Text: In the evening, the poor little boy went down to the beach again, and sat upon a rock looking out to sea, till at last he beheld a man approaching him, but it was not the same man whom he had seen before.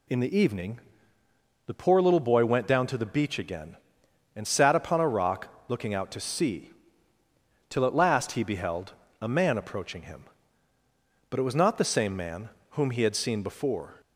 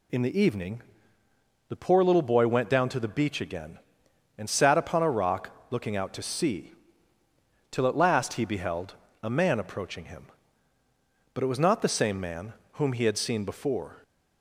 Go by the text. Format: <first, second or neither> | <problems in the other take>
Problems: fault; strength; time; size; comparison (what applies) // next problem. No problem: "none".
neither | pauses between "rock" and "looking"; slight; the same in both // pauses between "beheld" and "a"; slight; the same in both // pauses between "man" and "whom"; slight; the same in both